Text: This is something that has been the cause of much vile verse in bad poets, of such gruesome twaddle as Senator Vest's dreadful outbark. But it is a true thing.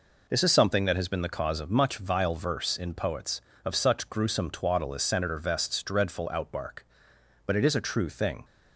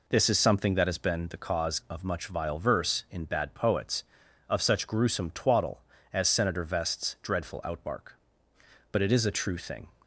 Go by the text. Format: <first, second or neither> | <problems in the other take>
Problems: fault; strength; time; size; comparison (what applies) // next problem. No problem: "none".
second | skips "bad"; at 2.9 s